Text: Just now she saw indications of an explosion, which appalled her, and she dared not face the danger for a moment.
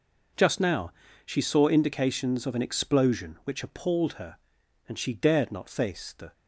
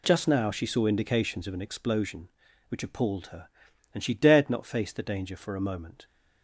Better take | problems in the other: second | pauses between "now" and "she"; slight; at 0.9 s; 0.34 s long // stops before "danger for a moment"; at 6.3 s

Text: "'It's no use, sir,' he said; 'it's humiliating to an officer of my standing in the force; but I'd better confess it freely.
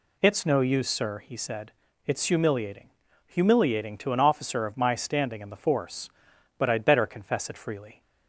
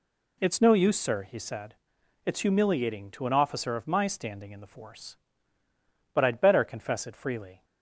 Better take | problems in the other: second | says "humiliating" twice; at 3.2 s

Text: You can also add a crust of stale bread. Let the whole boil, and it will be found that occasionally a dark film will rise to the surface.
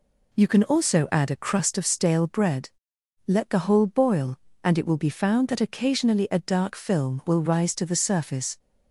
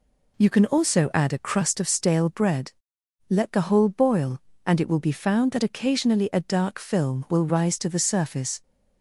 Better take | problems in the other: neither | none

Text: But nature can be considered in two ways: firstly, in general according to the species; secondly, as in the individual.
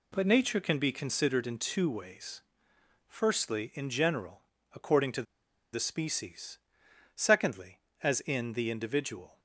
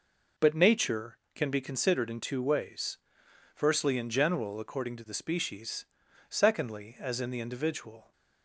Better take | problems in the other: second | pauses between "general" and "according"; slight; at 4.4 s; 0.34 s long // pauses between "to" and "the"; noticeable; at 5.2 s; 0.49 s long

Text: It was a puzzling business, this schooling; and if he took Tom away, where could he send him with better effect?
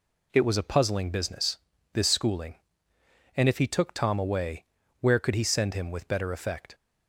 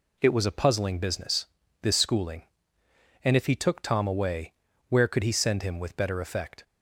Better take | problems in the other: neither | none

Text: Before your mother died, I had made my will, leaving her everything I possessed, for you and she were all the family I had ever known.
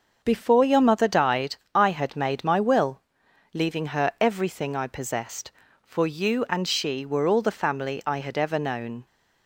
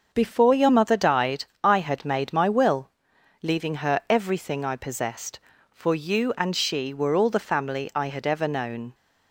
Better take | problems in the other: neither | starts louder than the rest; the same in both

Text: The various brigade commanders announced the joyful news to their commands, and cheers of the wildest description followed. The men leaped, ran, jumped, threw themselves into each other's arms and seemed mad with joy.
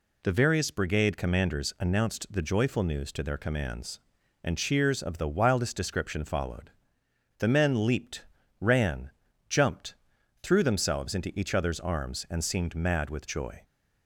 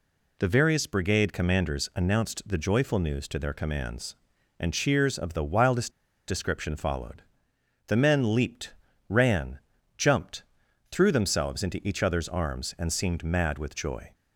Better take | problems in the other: first | pauses between "wildest" and "description"; at 5.9 s; 0.37 s long

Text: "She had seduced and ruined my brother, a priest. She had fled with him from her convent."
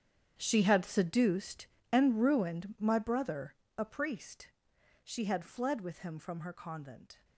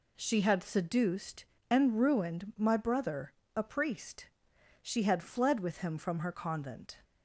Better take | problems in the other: second | gets quieter; strong; throughout; 15.5 dB

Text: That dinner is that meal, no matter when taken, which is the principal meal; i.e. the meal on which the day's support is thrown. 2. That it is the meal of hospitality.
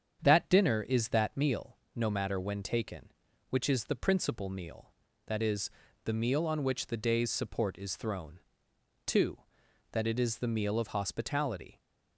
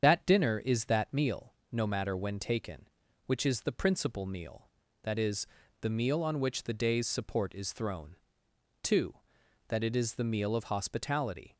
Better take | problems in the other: first | loses the start of "That"; at 0.0 s; 50 ms // starts louder than the rest; strong; until 1.0 s; 7.5 dB; strong in the first

